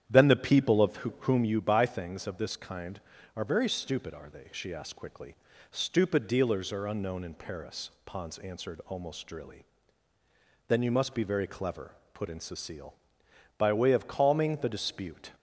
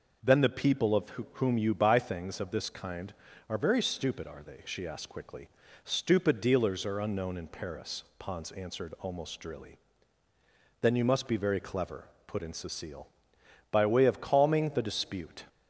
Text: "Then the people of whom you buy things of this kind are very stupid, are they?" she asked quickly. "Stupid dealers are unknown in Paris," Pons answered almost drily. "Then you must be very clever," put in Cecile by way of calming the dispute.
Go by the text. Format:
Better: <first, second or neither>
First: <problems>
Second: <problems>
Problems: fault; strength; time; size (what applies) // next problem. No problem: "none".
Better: second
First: starts louder than the rest; strong; until 1.5 s; 9.5 dB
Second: none